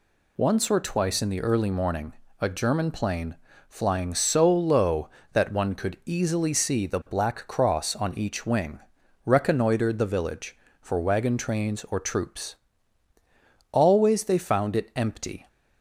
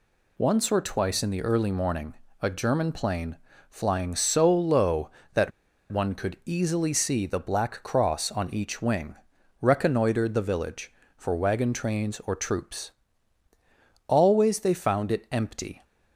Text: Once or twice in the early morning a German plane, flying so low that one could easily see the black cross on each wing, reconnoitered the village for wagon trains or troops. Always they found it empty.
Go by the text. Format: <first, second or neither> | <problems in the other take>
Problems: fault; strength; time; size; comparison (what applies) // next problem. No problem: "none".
first | pauses between "morning" and "a"; slight; at 2.1 s; 0.30 s long; slight in the first // pauses between "that" and "one"; at 5.5 s; 0.40 s long